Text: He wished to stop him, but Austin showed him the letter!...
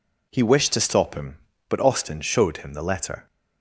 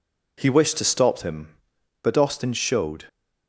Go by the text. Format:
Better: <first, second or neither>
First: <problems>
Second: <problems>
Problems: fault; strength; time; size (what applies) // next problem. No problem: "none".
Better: first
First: none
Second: stops before "him the letter"; at 3.0 s